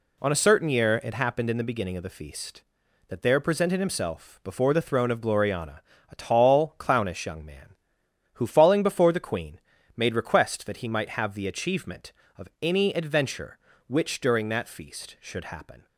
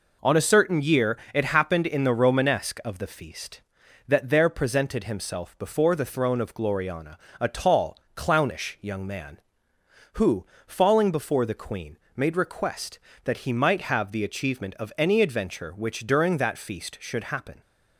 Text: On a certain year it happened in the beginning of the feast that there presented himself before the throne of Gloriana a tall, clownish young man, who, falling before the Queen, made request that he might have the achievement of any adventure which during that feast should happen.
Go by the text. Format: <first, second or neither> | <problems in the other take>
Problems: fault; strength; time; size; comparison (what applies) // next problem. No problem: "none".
first | pauses between "year" and "it"; slight; at 1.1 s; 0.16 s long // says "romanesque" for "beginning"; at 2.1 s // pauses between "Gloriana" and "a"; slight; at 7.1 s; 0.20 s long; slight in the first